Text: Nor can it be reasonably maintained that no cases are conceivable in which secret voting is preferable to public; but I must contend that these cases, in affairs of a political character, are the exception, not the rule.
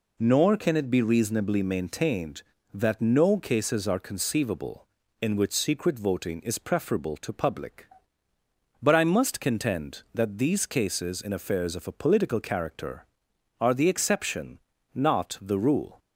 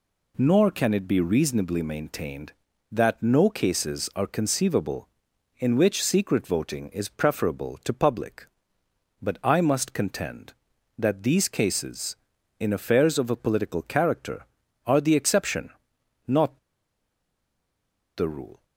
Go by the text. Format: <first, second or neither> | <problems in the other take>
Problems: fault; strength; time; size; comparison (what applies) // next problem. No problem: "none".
first | pauses between "not" and "the"; strong; at 16.5 s; 1.5 s long